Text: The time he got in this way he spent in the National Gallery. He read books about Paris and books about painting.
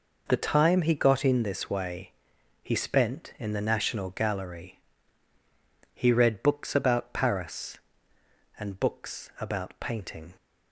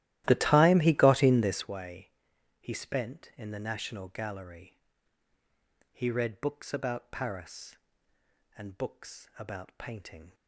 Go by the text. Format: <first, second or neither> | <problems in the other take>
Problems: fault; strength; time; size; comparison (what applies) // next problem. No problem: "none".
first | starts louder than the rest; strong; until 1.7 s; 14.5 dB // pauses between "way" and "he"; noticeable; at 2.0 s; 0.50 s long; noticeable in the first